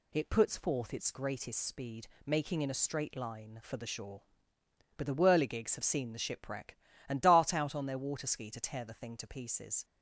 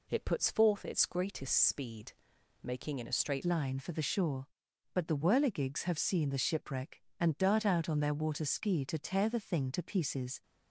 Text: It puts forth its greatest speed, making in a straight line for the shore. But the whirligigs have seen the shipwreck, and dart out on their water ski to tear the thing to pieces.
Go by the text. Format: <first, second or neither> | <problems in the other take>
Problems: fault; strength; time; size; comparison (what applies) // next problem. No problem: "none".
first | changes voice at "line"; from 3.4 s on; 7.0 s long